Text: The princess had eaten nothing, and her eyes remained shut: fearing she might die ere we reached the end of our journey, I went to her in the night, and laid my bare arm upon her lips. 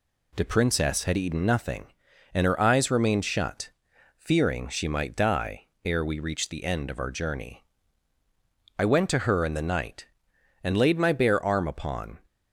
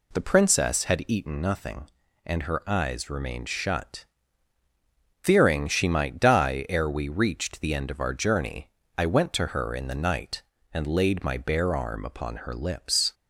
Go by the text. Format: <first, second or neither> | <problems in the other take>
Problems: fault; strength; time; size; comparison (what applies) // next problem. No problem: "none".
second | pauses between "die" and "ere"; slight; at 5.6 s; 0.16 s long // stops before "her lips"; at 12.2 s